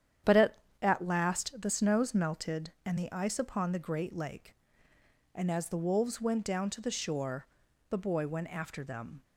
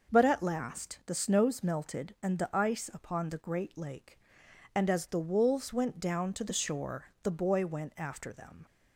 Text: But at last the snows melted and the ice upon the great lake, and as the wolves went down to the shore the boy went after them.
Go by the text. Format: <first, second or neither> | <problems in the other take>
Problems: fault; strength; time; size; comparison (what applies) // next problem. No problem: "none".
second | starts louder than the rest; strong; until 1.4 s; 9.5 dB // says "at" twice; at 0.8 s // pauses between "shore" and "the"; at 7.4 s; 0.42 s long; slight in the second